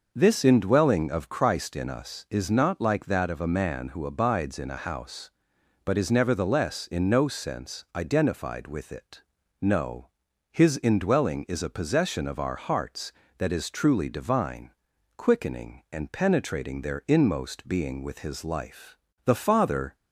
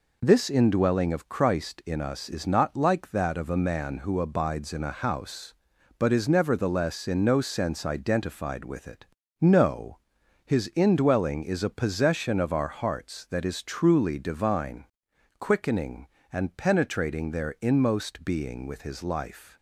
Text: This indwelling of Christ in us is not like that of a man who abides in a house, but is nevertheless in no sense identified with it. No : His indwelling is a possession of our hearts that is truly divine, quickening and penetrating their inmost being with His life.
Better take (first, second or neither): second